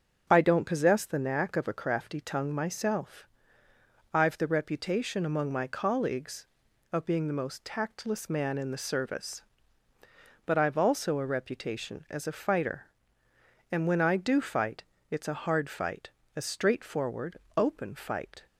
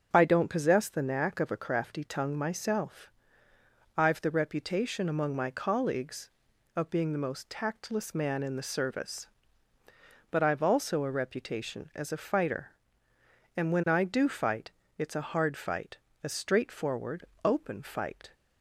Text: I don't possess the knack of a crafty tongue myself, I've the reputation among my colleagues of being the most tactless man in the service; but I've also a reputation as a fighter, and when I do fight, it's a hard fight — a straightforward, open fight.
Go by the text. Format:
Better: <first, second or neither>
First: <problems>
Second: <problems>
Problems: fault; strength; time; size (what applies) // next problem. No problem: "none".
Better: neither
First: starts louder than the rest; until 1.3 s; 6.5 dB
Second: starts louder than the rest; until 1.1 s; 6.5 dB